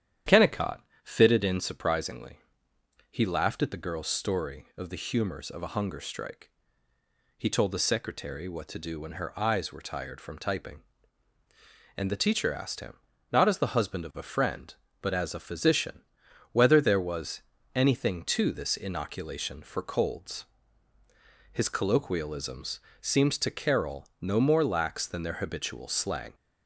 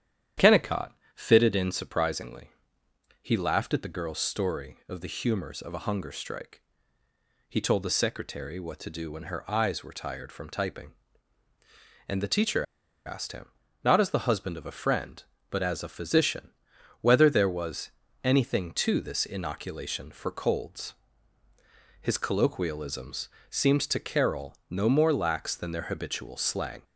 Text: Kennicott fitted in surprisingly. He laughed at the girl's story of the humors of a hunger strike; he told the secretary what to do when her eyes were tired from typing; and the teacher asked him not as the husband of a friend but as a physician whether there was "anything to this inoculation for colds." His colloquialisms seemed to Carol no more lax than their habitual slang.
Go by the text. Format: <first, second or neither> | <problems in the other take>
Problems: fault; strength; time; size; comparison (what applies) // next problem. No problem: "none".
first | starts louder than the rest; strong; until 1.6 s; 10 dB; strong in the first // pauses between "Kennicott" and "fitted"; slight; at 0.9 s; 0.24 s long; slight in the first // pauses between "teacher" and "asked"; at 12.6 s; 0.43 s long // pauses between "him" and "not"; slight; at 13.4 s; 0.34 s long; slight in the first // pauses between "physician" and "whether"; noticeable; at 16.5 s; 0.50 s long; noticeable in the first // pauses between "was" and "anything"; slight; at 17.8 s; 0.34 s long; slight in the first // pauses between "colloquialisms" and "seemed"; slight; at 23.2 s; 0.22 s long; slight in the first